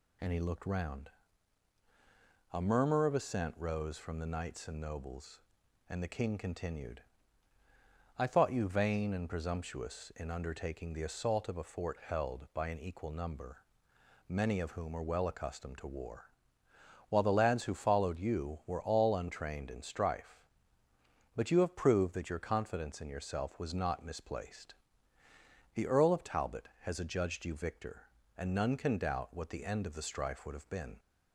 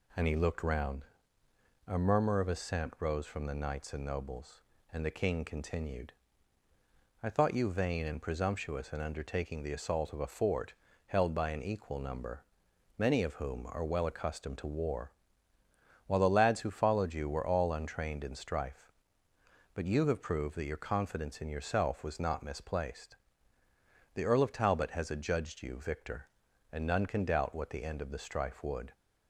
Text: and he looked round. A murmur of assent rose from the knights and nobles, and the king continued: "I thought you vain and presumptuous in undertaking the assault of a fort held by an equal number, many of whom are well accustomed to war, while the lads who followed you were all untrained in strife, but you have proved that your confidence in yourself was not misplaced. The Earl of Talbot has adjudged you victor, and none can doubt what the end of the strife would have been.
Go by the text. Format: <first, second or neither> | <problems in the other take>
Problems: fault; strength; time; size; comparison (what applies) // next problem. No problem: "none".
first | pauses between "fort" and "held"; slight; at 10.7 s; 0.34 s long // stops before "have been"; at 28.9 s